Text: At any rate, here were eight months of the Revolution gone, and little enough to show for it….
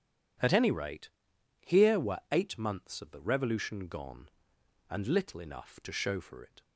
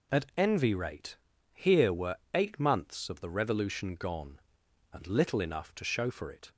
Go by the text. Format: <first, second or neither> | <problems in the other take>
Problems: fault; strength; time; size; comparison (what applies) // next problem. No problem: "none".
first | says "envy" for "any"; at 0.3 s // pauses between "were" and "eight"; slight; at 2.1 s; 0.18 s long